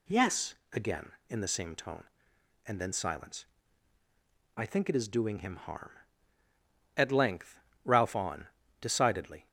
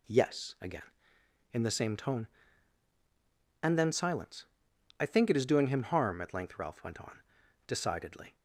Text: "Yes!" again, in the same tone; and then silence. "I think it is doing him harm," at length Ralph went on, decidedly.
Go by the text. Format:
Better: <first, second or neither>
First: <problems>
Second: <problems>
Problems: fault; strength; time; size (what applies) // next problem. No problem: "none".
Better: second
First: pauses between "length" and "Ralph"; slight; at 7.5 s; 0.24 s long // skips "went"; at 8.1 s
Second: none